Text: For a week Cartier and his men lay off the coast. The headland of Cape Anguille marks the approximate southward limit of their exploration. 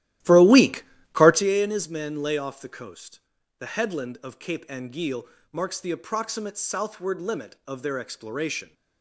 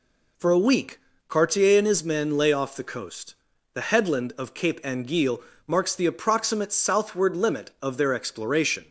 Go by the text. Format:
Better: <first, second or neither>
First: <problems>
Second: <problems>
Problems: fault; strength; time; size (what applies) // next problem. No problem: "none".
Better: second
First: starts louder than the rest; strong; until 1.5 s; 14 dB // pauses between "week" and "Cartier"; slight; at 0.8 s; 0.30 s long // pauses between "Anguille" and "marks"; slight; at 5.2 s; 0.24 s long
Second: pauses between "week" and "Cartier"; slight; at 0.9 s; 0.30 s long // pauses between "Anguille" and "marks"; slight; at 5.4 s; 0.24 s long